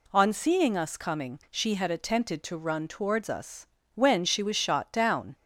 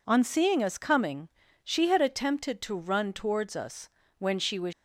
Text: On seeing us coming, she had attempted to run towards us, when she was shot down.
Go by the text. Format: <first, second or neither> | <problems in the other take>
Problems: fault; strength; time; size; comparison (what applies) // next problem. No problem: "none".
first | stops before "shot down"; at 4.7 s